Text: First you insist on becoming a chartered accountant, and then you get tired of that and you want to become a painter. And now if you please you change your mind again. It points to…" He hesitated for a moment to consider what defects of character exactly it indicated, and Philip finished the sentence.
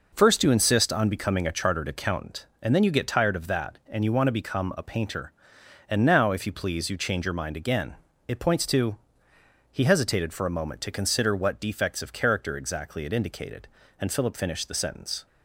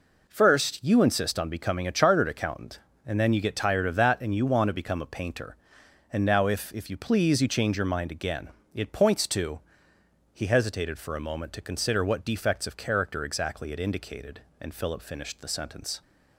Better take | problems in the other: first | says "if" twice; at 6.7 s

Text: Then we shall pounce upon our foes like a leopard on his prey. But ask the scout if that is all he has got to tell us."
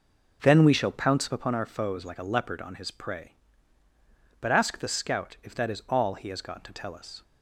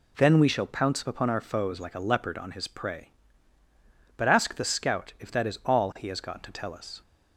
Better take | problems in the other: second | starts louder than the rest; noticeable; until 1.4 s; 5.5 dB

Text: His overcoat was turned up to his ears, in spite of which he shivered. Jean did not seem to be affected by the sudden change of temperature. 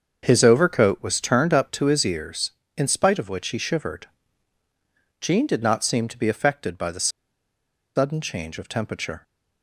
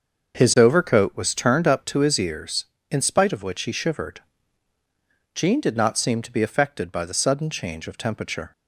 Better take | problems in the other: second | starts louder than the rest; until 1.2 s; 6.5 dB; also in the second // pauses between "the" and "sudden"; noticeable; at 7.0 s; 0.87 s long

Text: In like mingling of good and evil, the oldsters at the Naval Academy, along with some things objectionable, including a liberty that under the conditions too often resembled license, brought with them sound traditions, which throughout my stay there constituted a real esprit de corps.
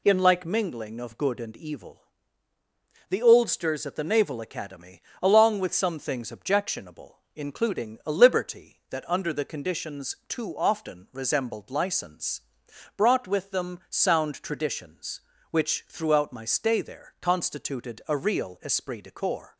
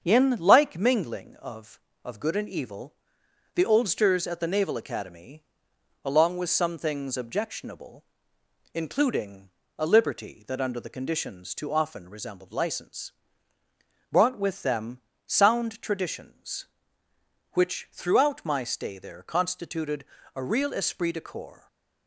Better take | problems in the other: first | starts louder than the rest; strong; until 1.0 s; 7 dB // says "of" twice; at 2.0 s // pauses between "including" and "a"; slight; at 9.4 s; 0.28 s long // pauses between "them" and "sound"; slight; at 15.0 s; 0.26 s long // pauses between "constituted" and "a"; slight; at 20.0 s; 0.32 s long

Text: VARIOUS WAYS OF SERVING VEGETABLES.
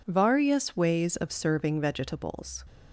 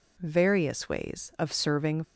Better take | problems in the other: first | stops before "VEGETABLES"; at 2.0 s

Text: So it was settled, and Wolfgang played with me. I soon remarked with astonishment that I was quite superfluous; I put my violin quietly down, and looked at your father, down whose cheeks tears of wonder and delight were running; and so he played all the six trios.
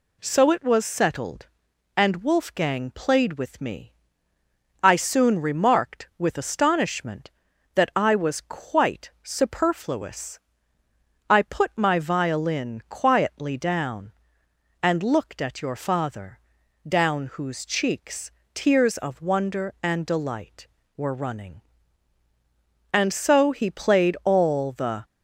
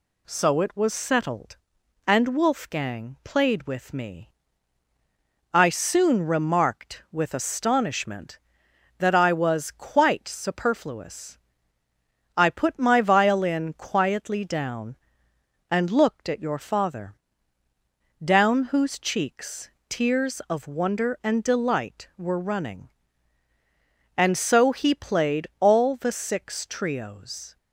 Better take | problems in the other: second | pauses between "cheeks" and "tears"; slight; at 18.3 s; 0.22 s long; slight in the second // stops before "six trios"; at 25.0 s

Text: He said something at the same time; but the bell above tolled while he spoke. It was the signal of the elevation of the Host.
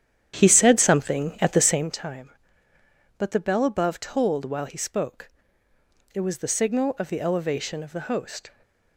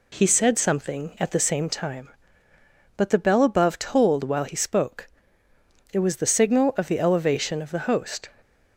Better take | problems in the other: second | starts louder than the rest; strong; until 1.9 s; 10 dB

